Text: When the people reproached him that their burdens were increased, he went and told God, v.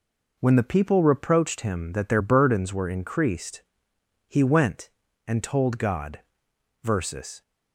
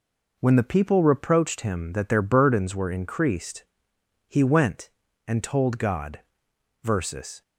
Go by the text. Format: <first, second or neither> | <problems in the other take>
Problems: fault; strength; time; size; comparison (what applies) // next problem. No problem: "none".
neither | none